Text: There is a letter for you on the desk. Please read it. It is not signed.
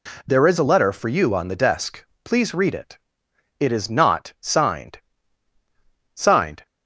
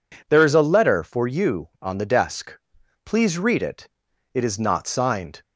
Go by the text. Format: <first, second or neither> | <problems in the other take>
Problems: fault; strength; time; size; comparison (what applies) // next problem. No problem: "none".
second | says "signed" twice; at 6.1 s